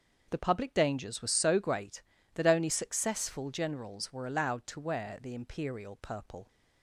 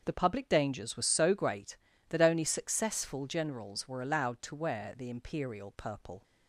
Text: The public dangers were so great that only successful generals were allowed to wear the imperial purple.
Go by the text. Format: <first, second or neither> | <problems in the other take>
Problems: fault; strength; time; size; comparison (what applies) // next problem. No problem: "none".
neither | starts louder than the rest; the same in both